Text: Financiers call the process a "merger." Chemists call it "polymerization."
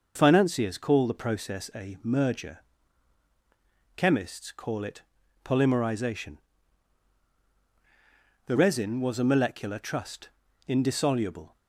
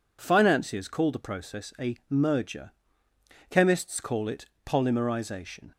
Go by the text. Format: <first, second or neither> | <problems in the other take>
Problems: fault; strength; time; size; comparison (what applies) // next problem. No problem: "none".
second | pauses between "it" and "polymerization"; at 5.0 s; 0.42 s long; slight in the second // goes on to say "The resin was a molecular trust indissoluble"; strong; from 8.4 s on; 3.1 s long